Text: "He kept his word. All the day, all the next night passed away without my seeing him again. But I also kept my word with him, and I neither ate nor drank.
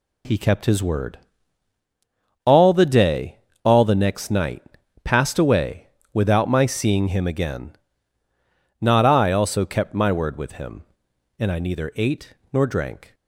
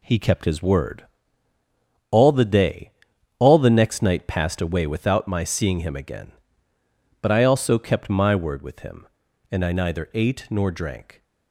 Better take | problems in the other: second | pauses between "night" and "passed"; at 4.6 s; 0.40 s long // pauses between "away" and "without"; slight; at 5.8 s; 0.26 s long // says "Not" for "But"; at 8.7 s // pauses between "ate" and "nor"; slight; at 12.3 s; 0.18 s long

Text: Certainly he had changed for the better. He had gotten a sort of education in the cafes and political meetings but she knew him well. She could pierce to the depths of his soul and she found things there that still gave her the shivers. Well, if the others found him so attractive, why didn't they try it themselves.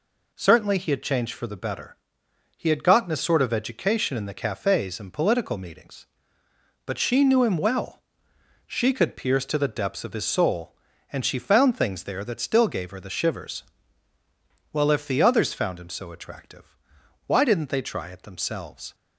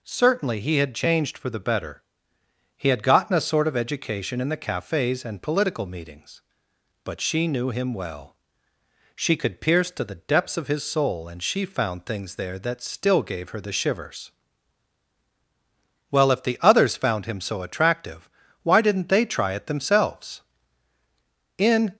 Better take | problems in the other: first | goes on to say "In"; slight; from 21.5 s on; 0.38 s long

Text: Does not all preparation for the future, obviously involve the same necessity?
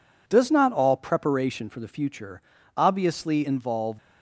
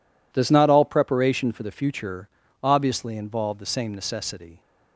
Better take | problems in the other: second | stops before "the same necessity"; at 3.9 s

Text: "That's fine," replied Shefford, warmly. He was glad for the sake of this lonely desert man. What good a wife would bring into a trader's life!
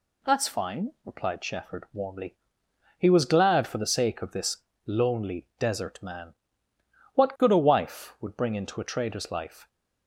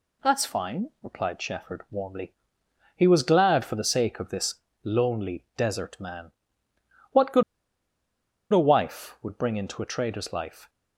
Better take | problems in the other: first | pauses between "this" and "lonely"; slight; at 4.5 s; 0.28 s long; slight in the first // pauses between "good" and "a"; at 7.4 s; 1.0 s long

